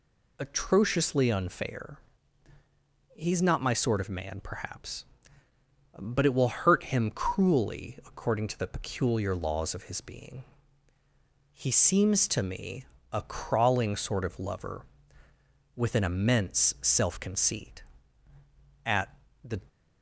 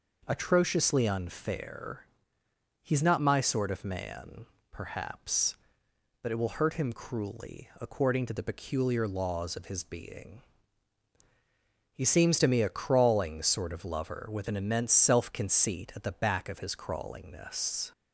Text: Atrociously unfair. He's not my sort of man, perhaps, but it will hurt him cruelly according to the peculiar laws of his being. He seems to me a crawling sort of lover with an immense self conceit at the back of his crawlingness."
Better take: second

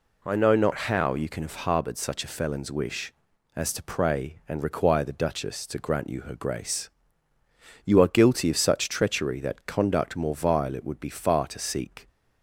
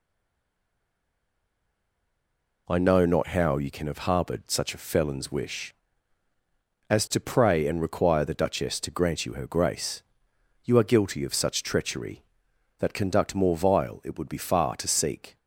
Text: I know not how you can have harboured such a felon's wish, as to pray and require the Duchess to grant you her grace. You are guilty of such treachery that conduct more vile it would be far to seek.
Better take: first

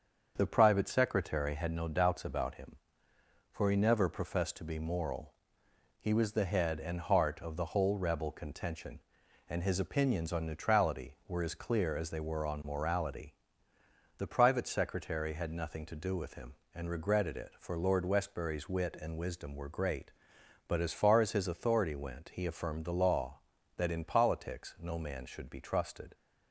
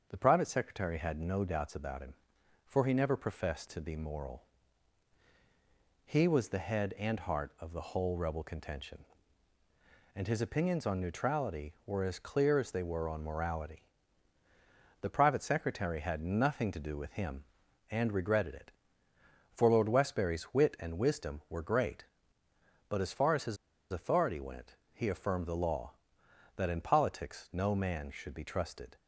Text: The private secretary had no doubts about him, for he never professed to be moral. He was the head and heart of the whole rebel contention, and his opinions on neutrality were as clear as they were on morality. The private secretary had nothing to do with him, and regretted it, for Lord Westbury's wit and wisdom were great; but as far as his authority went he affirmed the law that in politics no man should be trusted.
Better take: first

